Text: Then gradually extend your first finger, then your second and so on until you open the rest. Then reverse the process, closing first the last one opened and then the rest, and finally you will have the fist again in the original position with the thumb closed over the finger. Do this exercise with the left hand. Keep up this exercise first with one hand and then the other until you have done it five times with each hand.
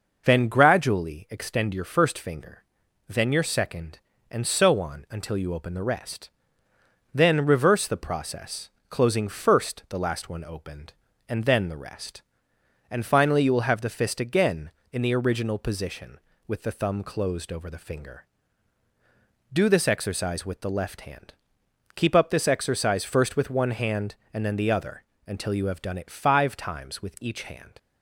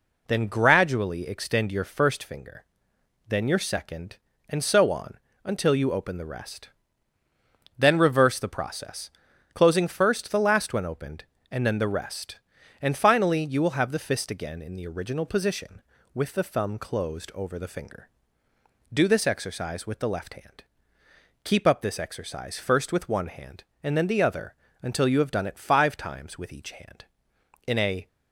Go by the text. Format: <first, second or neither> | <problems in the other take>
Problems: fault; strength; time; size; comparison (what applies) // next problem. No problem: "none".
first | pauses between "on" and "until"; slight; at 5.1 s; 0.26 s long // pauses between "other" and "until"; slight; at 24.5 s; 0.26 s long; slight in the first // goes on to say "In a"; slight; from 27.6 s on; 0.40 s long